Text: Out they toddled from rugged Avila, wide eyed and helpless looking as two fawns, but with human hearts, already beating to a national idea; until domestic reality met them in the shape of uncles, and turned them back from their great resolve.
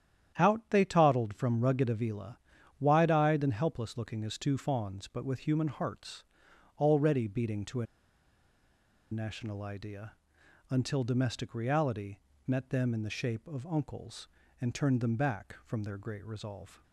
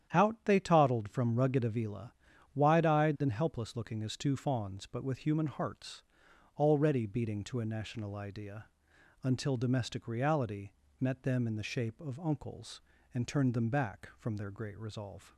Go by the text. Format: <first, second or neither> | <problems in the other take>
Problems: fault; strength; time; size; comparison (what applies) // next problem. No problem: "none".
second | starts louder than the rest; strong; until 1.3 s; 10 dB; strong in the second // pauses between "a" and "national"; strong; at 7.8 s; 1.2 s long // pauses between "reality" and "met"; slight; at 12.1 s; 0.28 s long; slight in the second